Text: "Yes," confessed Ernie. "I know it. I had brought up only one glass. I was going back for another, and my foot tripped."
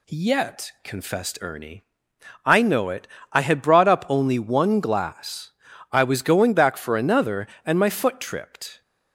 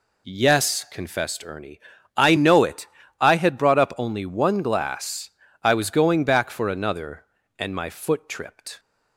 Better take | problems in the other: second | says "Yet" for "Yes"; at 0.0 s

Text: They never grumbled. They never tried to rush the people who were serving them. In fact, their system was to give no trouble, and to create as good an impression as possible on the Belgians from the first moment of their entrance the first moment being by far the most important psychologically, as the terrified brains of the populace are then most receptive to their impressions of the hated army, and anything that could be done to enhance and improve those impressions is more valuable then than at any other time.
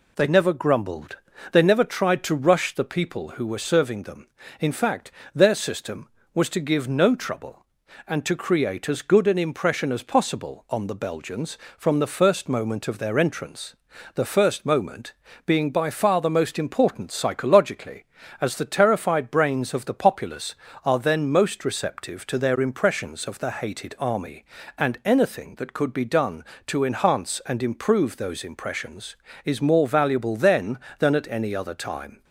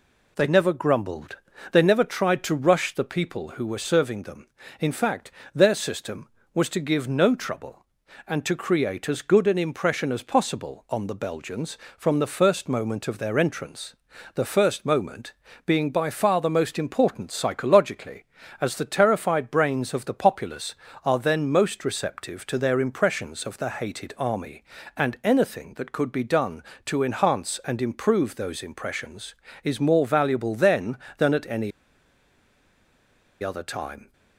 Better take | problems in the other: first | pauses between "entrance" and "the"; at 13.9 s; 0.40 s long; also in the first // pauses between "moment" and "being"; slight; at 15.3 s; 0.32 s long; slight in the first // pauses between "any" and "other"; strong; at 31.7 s; 1.7 s long

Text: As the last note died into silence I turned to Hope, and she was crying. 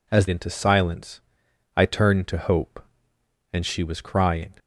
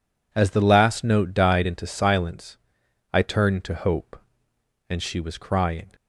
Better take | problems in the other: second | skips "the last note died"; at 0.2 s // pauses between "silence" and "I"; noticeable; at 1.1 s; 0.56 s long; noticeable in the second

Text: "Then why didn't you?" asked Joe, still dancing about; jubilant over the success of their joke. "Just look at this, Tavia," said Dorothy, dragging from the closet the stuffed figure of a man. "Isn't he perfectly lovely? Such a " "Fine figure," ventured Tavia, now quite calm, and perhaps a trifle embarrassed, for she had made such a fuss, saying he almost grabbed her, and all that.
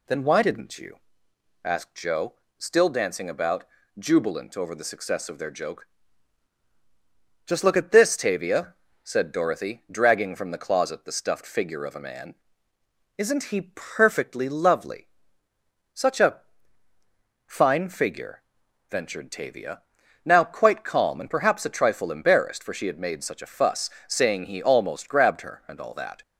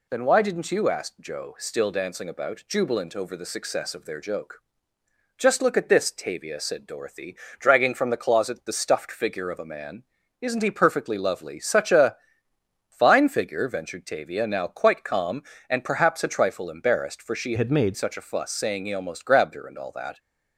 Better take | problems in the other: first | changes voice from "had" to "made"; from 17.5 to 17.9 s; 0.4 s long

